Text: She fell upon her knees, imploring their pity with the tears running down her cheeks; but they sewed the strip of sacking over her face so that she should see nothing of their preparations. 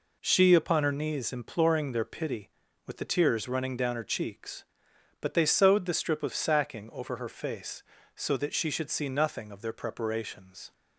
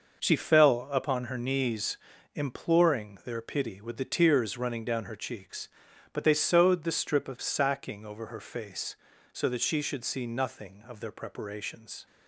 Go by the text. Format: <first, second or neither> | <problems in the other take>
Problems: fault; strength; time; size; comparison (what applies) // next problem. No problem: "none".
second | skips "fell"; at 0.5 s